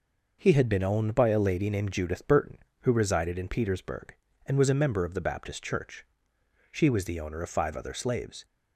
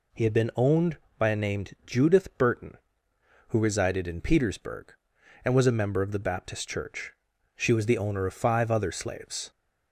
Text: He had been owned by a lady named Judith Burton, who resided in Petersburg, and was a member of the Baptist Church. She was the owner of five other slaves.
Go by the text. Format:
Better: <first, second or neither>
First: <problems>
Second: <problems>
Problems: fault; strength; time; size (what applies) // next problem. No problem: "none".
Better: first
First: none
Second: skips "lady"; at 1.3 s